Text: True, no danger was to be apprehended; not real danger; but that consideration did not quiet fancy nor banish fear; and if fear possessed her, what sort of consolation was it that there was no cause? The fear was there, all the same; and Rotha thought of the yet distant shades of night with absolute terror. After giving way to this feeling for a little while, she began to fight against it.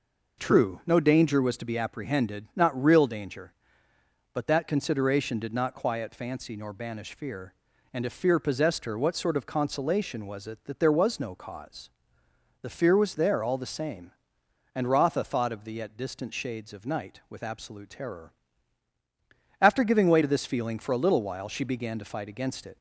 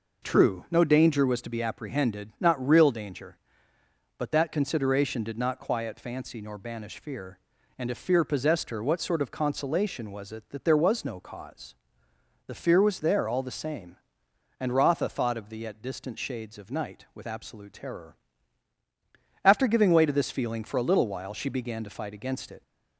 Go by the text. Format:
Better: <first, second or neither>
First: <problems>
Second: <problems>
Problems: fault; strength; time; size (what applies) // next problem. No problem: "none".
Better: neither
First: none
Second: none